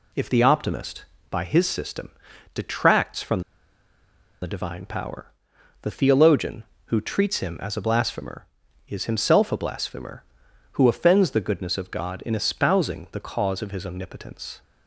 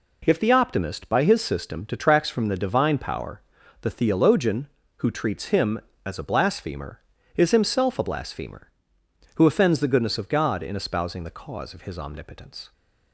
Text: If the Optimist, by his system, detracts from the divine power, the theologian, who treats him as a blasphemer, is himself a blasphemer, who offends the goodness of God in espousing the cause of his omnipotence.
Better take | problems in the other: second | pauses between "from" and "the"; at 3.4 s; 1.0 s long

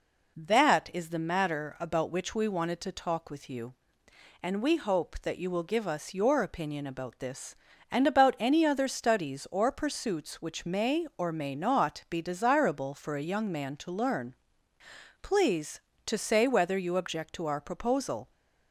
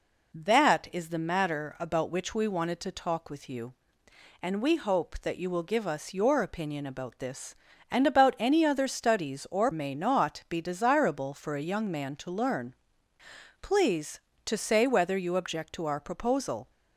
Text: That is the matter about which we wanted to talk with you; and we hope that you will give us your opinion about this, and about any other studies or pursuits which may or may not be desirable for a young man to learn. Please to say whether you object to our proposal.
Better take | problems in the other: first | skips "pursuits which may or"; at 9.7 s

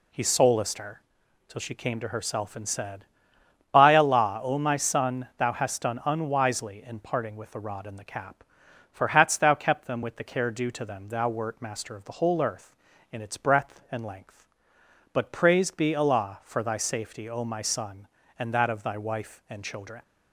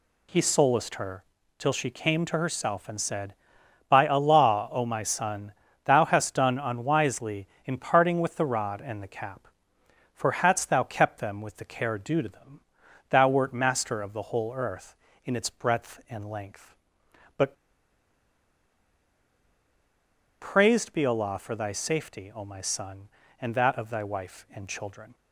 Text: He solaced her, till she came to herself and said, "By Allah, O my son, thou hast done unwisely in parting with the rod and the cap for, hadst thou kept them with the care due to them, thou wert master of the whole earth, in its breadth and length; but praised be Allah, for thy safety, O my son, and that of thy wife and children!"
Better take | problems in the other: first | pauses between "but" and "praised"; strong; at 17.5 s; 2.8 s long

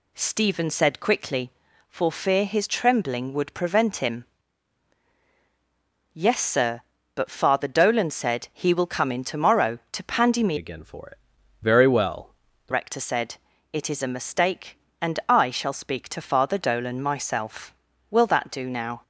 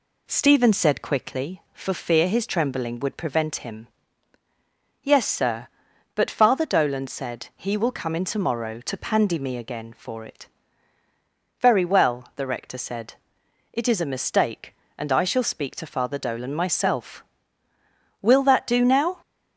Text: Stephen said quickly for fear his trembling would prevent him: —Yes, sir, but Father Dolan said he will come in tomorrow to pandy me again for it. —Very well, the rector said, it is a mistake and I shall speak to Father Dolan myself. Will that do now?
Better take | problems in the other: second | changes voice from "again" to "the"; from 10.5 to 12.7 s; 2.2 s long

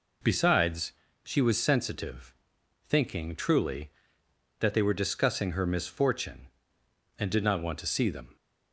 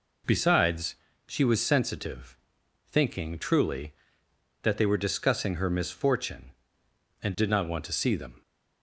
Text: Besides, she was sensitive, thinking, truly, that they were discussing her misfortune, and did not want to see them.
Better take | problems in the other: neither | none

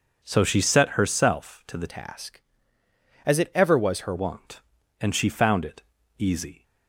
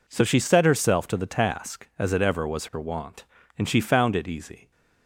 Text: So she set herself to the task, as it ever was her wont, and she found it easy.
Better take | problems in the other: second | changes voice from "task" to "her"; from 1.8 to 4.1 s; 2.3 s long // pauses between "it" and "easy"; slight; at 5.8 s; 0.34 s long

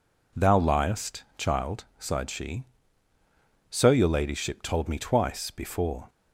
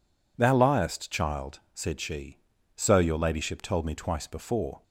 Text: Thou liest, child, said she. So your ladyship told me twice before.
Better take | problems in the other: second | says "sighed" for "said"; at 1.9 s

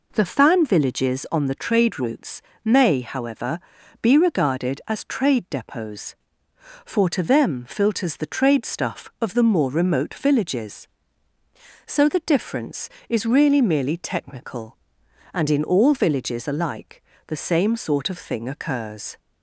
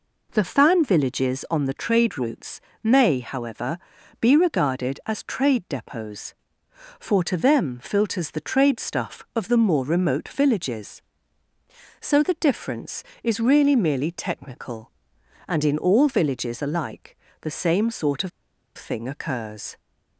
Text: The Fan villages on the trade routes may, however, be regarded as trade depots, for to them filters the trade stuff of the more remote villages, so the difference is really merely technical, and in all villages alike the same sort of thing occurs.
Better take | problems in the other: first | pauses between "routes" and "may"; slight; at 2.6 s; 0.24 s long; slight in the first // pauses between "alike" and "the"; slight; at 17.1 s; 0.24 s long; slight in the first // pauses between "of" and "thing"; noticeable; at 18.3 s; 0.47 s long

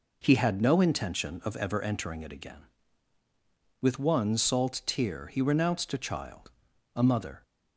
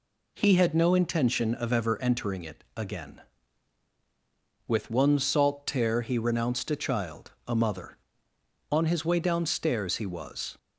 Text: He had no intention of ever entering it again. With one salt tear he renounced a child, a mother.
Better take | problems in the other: first | goes on to say "On his way downstairs he was"; strong; from 8.7 s on; 1.8 s long

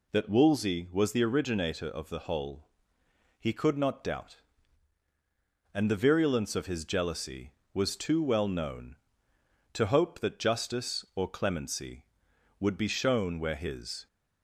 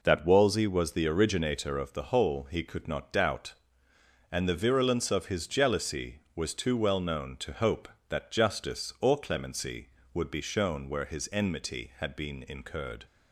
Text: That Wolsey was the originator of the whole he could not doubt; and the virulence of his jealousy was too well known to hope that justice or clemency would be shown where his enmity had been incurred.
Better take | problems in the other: second | pauses between "whole" and "he"; noticeable; at 2.6 s; 0.76 s long // stops before "enmity had been incurred"; at 14.0 s

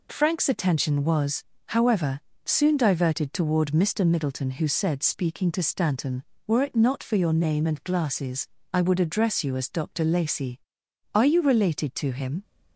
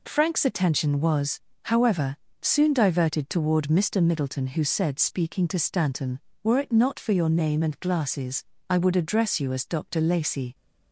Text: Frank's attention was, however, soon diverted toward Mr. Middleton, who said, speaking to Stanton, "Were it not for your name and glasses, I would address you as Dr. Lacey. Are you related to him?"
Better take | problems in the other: first | stops before "Are you related to him"; at 10.5 s

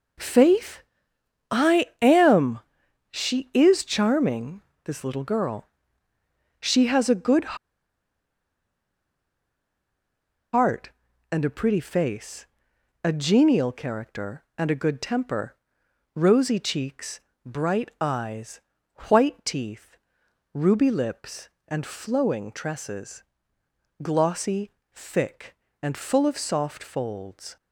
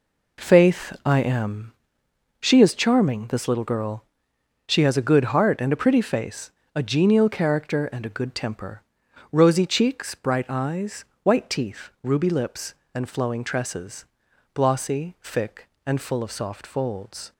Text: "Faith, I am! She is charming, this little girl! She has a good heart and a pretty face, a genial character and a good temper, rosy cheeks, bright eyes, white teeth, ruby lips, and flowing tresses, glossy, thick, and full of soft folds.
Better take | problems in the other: second | pauses between "good" and "heart"; strong; at 7.5 s; 2.9 s long

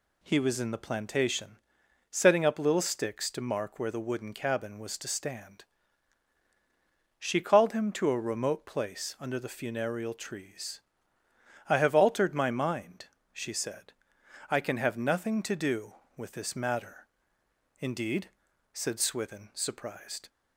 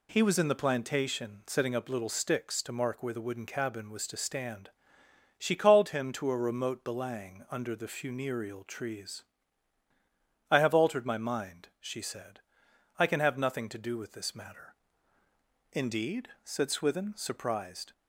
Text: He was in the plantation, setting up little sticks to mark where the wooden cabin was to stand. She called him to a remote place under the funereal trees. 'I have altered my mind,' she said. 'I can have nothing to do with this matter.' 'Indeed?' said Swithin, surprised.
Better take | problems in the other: first | says "belang" for "place"; at 6.8 s

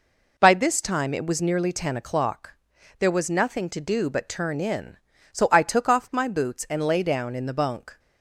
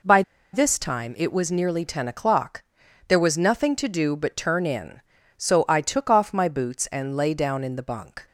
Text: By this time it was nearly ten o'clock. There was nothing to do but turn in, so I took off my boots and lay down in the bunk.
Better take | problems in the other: first | pauses between "By" and "this"; slight; at 0.2 s; 0.31 s long

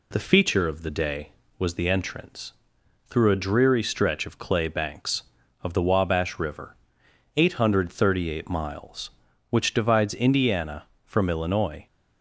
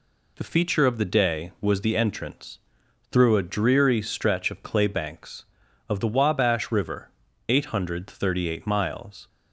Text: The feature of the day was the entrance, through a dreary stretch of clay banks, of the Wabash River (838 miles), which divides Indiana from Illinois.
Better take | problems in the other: first | stops before "which divides Indiana from Illinois"; at 9.2 s

